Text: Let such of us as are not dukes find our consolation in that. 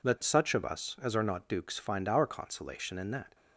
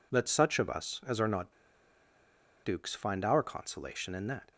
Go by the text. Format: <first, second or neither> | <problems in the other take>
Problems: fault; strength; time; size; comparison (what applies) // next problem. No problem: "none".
first | pauses between "not" and "dukes"; at 1.5 s; 1.1 s long